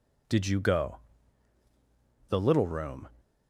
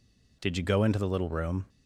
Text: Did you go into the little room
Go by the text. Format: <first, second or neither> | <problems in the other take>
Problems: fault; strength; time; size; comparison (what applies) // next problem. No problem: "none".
second | skips "into"; at 1.6 s